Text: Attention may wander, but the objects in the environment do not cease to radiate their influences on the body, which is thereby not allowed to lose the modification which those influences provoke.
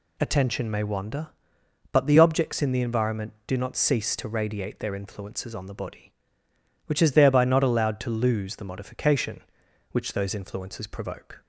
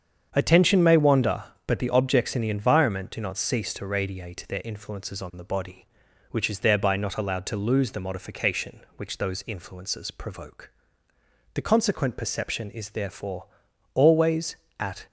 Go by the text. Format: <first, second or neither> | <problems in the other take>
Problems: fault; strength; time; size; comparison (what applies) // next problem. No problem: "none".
first | starts louder than the rest; strong; until 1.3 s; 7.5 dB // goes on to say "The consequent perception is therefore always at"; strong; from 11.5 s on; 3.5 s long